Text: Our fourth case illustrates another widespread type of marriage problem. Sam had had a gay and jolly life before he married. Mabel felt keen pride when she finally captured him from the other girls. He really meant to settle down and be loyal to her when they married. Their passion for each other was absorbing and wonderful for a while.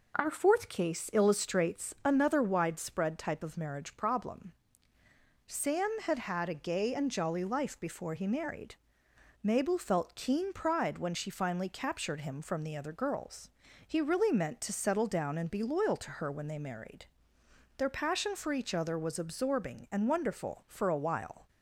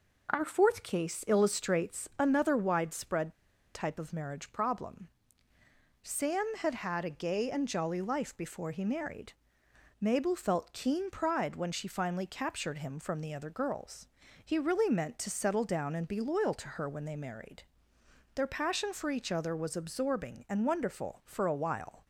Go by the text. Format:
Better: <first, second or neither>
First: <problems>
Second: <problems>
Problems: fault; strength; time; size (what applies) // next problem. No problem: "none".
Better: first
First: none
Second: pauses between "widespread" and "type"; at 3.3 s; 0.42 s long